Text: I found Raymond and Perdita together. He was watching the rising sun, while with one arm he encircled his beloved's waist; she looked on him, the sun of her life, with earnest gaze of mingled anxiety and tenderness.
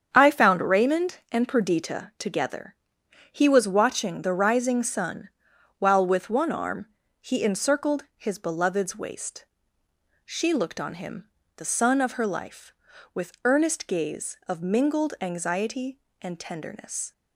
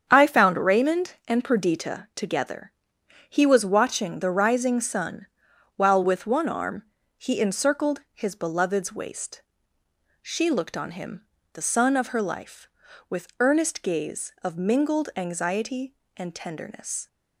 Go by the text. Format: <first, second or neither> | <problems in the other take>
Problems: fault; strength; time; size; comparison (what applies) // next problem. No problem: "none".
neither | starts louder than the rest; strong; the same in both // pauses between "arm" and "he"; slight; the same in both